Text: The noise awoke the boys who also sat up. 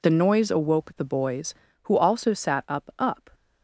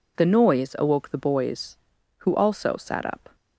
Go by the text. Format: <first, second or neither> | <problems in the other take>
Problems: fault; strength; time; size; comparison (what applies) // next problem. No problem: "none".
second | says "up" twice; at 2.9 s